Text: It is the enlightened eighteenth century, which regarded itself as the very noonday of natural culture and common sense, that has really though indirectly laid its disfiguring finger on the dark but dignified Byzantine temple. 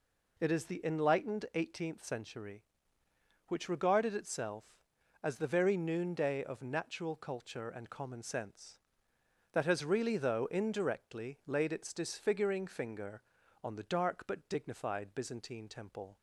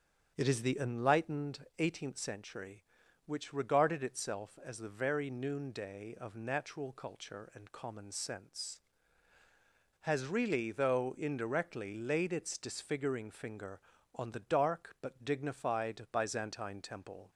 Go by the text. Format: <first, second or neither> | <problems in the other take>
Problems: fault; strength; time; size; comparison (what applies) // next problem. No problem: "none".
first | starts louder than the rest; strong; until 1.3 s; 8 dB // skips "that"; at 9.4 s